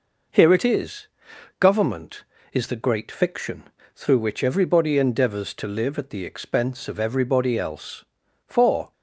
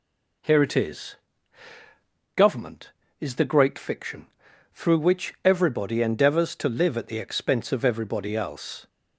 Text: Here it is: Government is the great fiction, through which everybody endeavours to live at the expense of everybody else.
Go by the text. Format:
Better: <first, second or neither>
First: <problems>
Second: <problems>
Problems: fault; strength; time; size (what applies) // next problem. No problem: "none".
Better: second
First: goes on to say "For"; slight; from 8.4 s on; 0.46 s long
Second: none